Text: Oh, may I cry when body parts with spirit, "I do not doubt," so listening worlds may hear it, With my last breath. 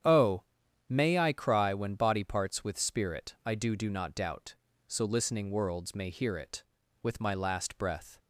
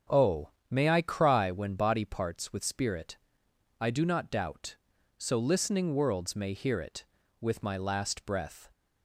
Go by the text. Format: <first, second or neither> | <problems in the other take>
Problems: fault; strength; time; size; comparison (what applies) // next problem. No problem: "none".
second | starts louder than the rest; strong; until 1.4 s; 9 dB; strong in the second // says "do" twice; at 3.7 s